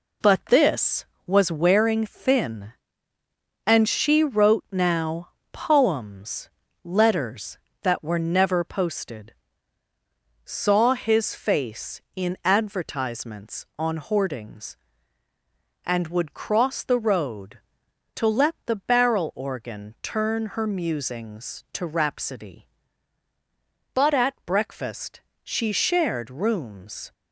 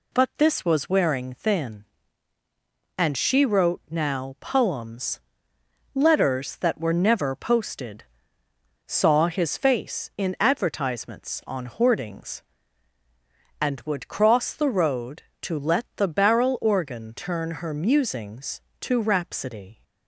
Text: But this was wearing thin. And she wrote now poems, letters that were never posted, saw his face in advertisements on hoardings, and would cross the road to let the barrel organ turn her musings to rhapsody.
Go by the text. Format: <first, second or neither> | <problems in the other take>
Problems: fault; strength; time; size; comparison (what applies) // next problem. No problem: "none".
second | pauses between "now" and "poems"; slight; at 5.2 s; 0.22 s long // goes on to say "But at breakfast she shared rooms"; strong; from 23.9 s on; 3.1 s long